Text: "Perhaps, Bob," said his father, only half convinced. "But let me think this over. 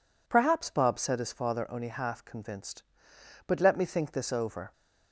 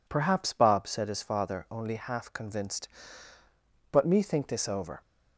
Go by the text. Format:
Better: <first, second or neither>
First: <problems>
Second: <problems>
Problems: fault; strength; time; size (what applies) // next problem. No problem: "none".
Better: first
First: none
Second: skips "let"; at 4.0 s